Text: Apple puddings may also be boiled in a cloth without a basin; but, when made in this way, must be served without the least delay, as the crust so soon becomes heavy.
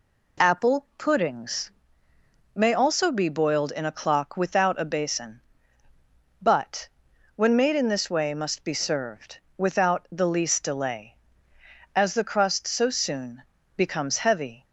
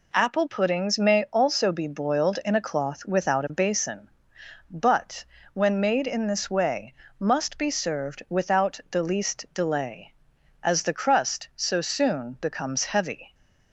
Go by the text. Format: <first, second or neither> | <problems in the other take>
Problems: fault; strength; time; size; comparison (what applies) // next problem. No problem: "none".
second | pauses between "puddings" and "may"; noticeable; at 1.6 s; 0.86 s long // says "clock" for "cloth"; at 3.9 s // pauses between "served" and "without"; slight; at 9.4 s; 0.16 s long // pauses between "soon" and "becomes"; slight; at 13.4 s; 0.34 s long